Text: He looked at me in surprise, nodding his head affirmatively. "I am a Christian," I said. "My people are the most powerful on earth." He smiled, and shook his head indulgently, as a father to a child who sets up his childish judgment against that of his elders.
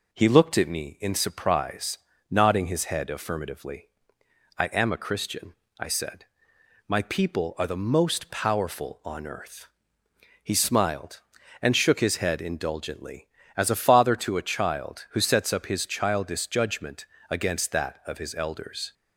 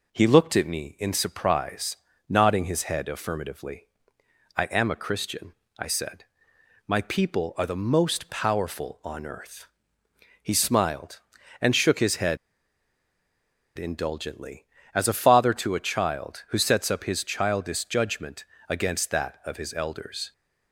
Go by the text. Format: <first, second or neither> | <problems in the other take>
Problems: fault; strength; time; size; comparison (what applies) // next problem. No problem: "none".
first | pauses between "head" and "indulgently"; strong; at 12.3 s; 1.4 s long // pauses between "judgment" and "against"; slight; at 18.4 s; 0.24 s long; slight in the first